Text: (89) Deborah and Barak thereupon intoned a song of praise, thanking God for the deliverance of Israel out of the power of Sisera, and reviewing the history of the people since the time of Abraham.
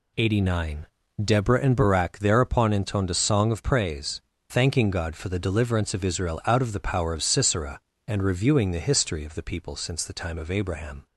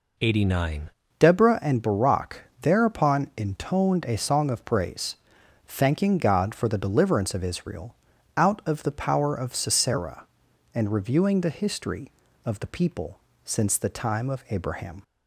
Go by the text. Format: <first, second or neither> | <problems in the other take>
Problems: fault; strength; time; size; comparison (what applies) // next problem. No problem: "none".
first | changes voice at "Deborah"; from 1.1 s on; 13.9 s long // pauses between "Barak" and "thereupon"; slight; at 2.4 s; 0.20 s long // pauses between "Israel" and "out"; at 7.9 s; 0.42 s long // pauses between "people" and "since"; slight; at 13.1 s; 0.26 s long